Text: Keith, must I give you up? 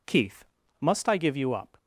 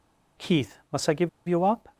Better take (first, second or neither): first